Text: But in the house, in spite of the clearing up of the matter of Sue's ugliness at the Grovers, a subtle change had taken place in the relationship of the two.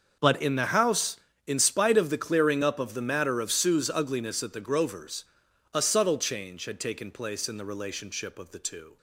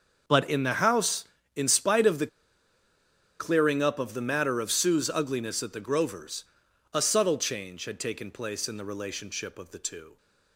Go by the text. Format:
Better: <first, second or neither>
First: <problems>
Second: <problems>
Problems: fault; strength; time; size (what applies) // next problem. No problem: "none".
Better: first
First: starts louder than the rest; until 1.4 s; 6.5 dB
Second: starts louder than the rest; until 1.5 s; 6.5 dB // pauses between "the" and "clearing"; at 2.2 s; 1.1 s long